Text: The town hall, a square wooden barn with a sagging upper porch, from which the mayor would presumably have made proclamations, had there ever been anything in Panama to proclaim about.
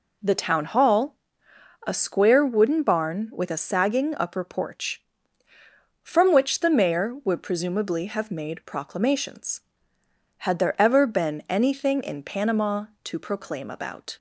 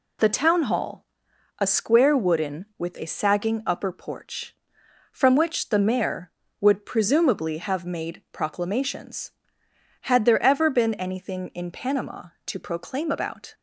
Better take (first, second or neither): first